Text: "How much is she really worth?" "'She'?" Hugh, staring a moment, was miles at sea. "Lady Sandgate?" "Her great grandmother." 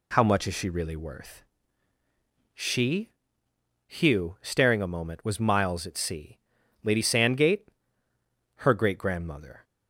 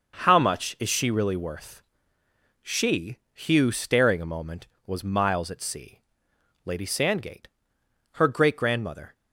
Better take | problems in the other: neither | none

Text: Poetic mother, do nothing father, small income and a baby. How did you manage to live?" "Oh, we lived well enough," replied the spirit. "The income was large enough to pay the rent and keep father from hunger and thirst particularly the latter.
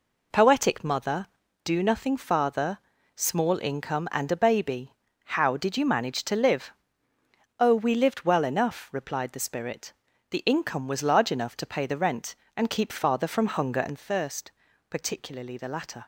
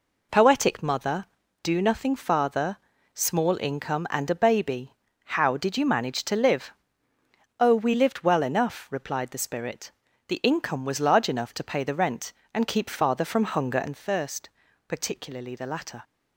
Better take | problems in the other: neither | pauses between "thirst" and "particularly"; the same in both

